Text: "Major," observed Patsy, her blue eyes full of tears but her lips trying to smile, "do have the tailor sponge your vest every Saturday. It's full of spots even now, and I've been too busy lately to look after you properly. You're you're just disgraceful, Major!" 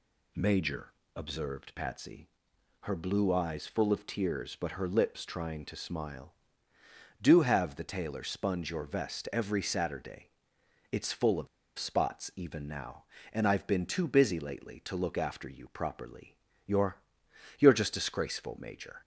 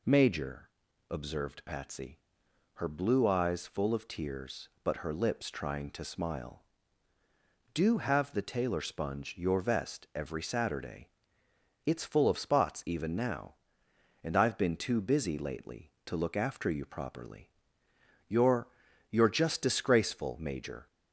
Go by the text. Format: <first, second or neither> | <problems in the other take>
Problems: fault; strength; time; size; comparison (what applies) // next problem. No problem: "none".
second | pauses between "of" and "spots"; slight; at 11.4 s; 0.31 s long // pauses between "You're" and "you're"; noticeable; at 16.9 s; 0.60 s long; also in the second